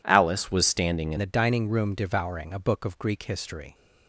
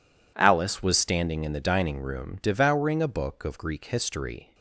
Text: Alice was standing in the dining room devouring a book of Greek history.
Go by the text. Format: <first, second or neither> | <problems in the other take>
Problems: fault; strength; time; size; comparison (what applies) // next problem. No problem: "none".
second | changes voice at "the"; from 1.1 s on; 2.6 s long